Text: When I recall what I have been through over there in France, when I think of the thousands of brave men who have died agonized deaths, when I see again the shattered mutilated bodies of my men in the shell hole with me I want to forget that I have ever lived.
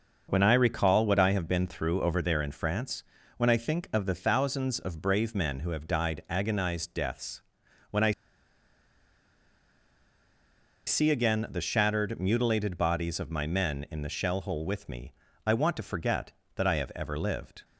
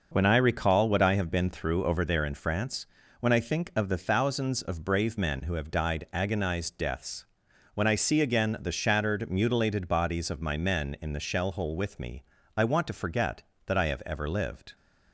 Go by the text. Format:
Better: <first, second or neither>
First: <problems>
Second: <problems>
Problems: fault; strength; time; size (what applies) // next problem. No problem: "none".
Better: second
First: pauses between "I" and "see"; strong; at 8.1 s; 2.7 s long // pauses between "me" and "I"; slight; at 15.1 s; 0.34 s long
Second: pauses between "me" and "I"; slight; at 12.2 s; 0.34 s long